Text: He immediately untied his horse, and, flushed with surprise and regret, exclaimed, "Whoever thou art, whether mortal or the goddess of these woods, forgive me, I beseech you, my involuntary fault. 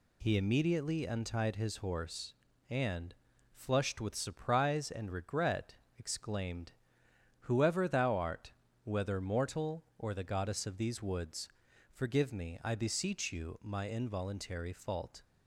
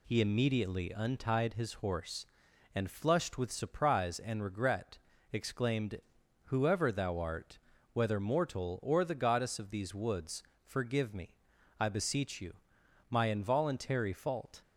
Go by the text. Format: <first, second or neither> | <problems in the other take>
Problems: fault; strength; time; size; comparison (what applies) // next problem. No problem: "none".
neither | none